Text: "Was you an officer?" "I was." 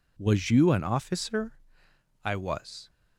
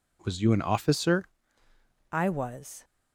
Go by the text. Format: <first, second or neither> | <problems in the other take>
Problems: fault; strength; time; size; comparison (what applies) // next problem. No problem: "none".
first | changes voice at "I"; from 2.1 s on; 0.7 s long